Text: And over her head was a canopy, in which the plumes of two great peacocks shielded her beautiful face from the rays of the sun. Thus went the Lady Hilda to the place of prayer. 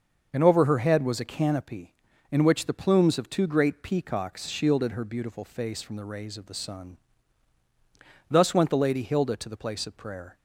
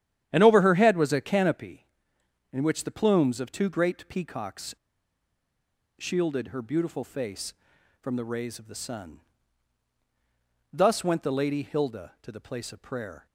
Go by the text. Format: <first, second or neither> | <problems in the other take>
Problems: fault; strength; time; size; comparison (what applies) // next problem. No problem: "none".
first | starts louder than the rest; strong; until 1.3 s; 10.5 dB; also in the first // pauses between "peacocks" and "shielded"; at 4.7 s; 1.2 s long